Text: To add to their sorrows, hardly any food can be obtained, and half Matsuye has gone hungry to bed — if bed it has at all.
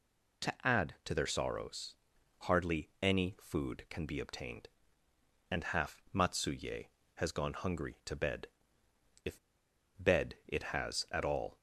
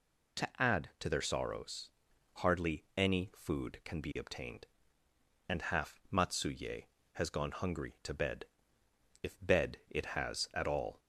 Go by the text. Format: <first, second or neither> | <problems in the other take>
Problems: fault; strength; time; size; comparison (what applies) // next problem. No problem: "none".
second | pauses between "if" and "bed"; noticeable; at 9.3 s; 0.63 s long